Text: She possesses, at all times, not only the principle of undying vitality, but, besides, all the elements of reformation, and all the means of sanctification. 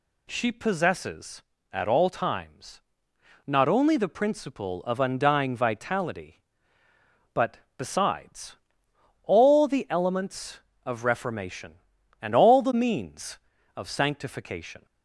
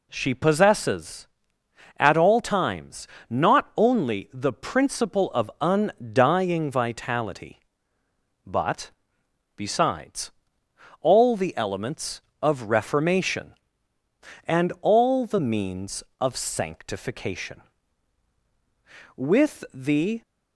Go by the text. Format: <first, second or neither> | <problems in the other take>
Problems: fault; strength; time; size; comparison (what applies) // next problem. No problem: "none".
first | goes on to say "With the"; noticeable; from 19.1 s on; 1.0 s long